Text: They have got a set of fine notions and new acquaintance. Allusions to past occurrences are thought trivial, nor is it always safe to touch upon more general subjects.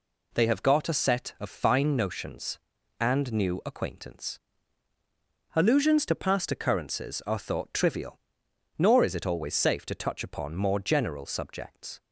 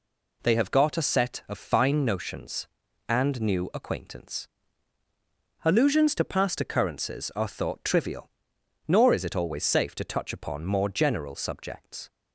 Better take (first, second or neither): neither